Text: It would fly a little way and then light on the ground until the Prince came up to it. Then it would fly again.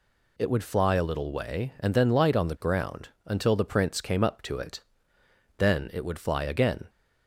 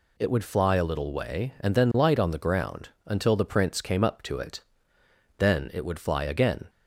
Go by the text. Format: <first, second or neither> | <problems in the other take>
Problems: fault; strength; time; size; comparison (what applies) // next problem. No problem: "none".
neither | pauses between "ground" and "until"; slight; the same in both